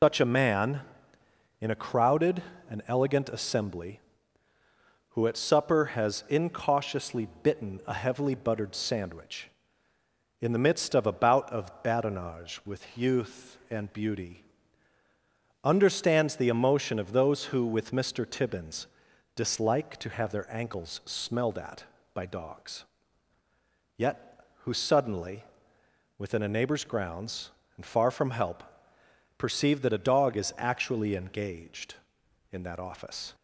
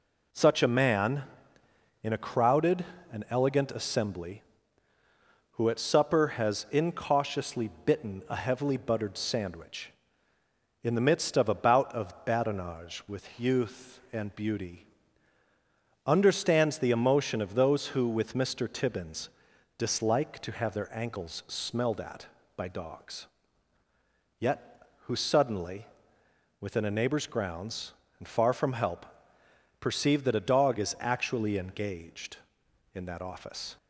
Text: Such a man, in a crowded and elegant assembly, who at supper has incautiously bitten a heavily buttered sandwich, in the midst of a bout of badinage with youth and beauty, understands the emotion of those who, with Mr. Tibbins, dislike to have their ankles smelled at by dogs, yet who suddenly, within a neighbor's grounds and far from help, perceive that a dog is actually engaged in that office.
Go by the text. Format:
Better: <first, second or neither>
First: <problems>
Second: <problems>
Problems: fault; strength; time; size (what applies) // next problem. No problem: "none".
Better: second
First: loses the start of "Such"; at 0.0 s; 115 ms // pauses between "incautiously" and "bitten"; slight; at 7.2 s; 0.16 s long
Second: pauses between "incautiously" and "bitten"; slight; at 7.6 s; 0.16 s long